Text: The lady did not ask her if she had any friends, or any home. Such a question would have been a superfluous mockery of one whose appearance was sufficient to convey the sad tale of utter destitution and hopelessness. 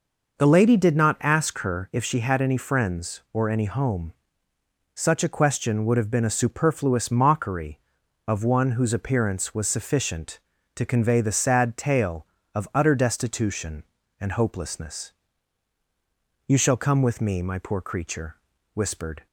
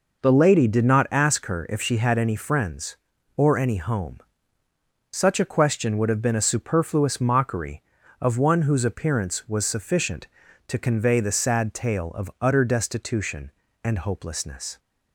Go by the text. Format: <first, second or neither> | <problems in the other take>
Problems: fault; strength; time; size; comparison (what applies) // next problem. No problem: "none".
second | goes on to say "You shall come with me my poor creature whispered"; strong; from 16.4 s on; 2.8 s long